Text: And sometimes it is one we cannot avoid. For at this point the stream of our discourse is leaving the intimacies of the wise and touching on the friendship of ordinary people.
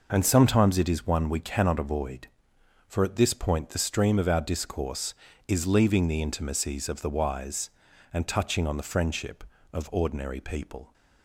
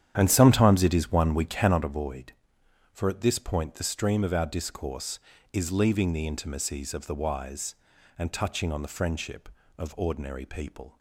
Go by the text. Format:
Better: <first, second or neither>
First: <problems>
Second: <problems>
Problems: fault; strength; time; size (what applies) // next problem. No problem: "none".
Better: first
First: none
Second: starts louder than the rest; strong; until 1.9 s; 9.5 dB